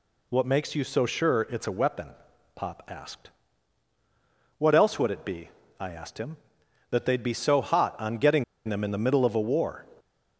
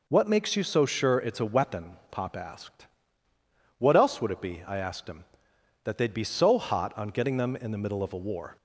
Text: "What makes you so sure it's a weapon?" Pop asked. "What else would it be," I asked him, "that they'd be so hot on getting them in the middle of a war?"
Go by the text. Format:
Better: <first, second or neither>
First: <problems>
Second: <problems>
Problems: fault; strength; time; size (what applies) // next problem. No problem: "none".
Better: second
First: pauses between "getting" and "them"; slight; at 8.4 s; 0.23 s long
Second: none